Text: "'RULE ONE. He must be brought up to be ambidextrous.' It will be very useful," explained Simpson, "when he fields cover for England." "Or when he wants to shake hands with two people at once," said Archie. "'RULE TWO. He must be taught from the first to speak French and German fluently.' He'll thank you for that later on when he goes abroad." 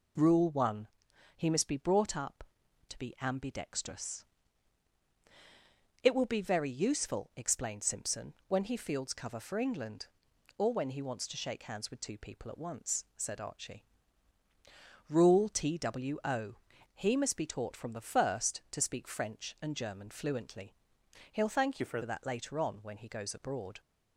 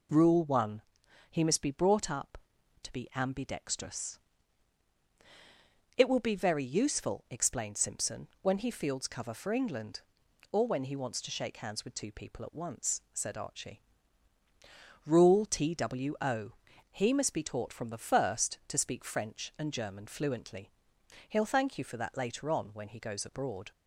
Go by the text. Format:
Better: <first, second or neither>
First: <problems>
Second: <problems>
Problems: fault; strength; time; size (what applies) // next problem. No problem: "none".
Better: second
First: changes voice from "you" to "for"; from 21.7 to 22.0 s; 0.3 s long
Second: none